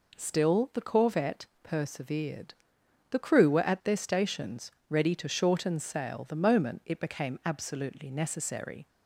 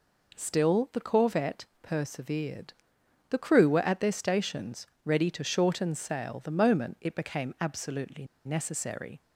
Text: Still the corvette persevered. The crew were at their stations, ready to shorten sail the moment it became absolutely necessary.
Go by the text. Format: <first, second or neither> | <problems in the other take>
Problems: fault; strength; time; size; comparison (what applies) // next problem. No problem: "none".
first | pauses between "corvette" and "persevered"; slight; at 1.6 s; 0.16 s long; slight in the first // pauses between "absolutely" and "necessary"; slight; at 8.2 s; 0.20 s long